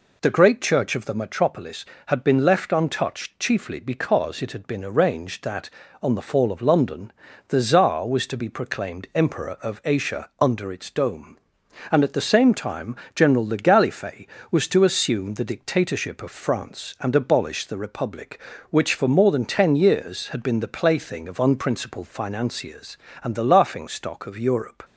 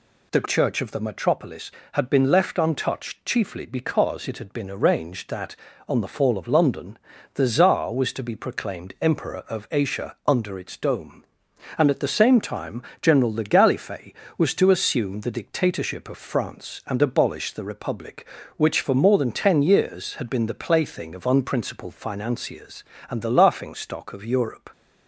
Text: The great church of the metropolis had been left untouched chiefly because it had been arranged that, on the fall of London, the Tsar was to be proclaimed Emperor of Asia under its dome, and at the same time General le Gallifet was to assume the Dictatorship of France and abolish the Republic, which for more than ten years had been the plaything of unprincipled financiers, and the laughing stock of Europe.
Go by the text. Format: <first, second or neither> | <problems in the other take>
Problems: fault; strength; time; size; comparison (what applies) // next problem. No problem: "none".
first | skips "great"; at 0.4 s // pauses between "time" and "General"; slight; at 12.8 s; 0.18 s long; slight in the first